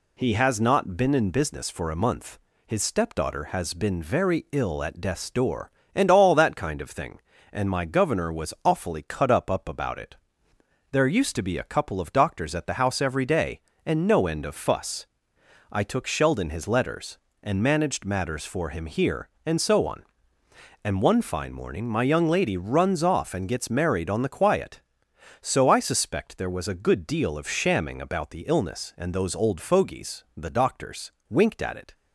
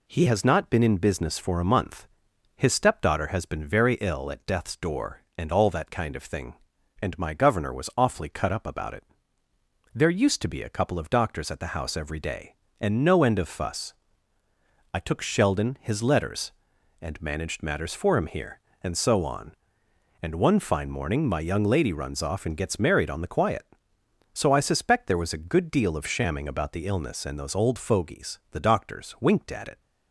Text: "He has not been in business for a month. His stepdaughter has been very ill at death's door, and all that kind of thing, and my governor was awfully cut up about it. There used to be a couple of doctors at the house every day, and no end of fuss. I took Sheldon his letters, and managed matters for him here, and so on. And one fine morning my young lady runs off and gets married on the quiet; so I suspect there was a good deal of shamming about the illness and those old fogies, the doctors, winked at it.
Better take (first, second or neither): second